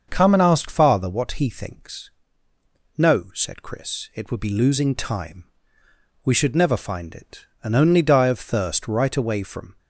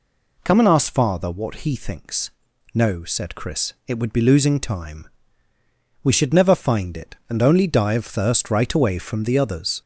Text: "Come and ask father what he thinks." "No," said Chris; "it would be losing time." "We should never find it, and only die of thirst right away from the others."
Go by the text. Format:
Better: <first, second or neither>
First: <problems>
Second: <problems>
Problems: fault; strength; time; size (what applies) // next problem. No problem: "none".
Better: second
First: starts louder than the rest; until 1.1 s; 6.5 dB // stops before "the others"; at 9.7 s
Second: none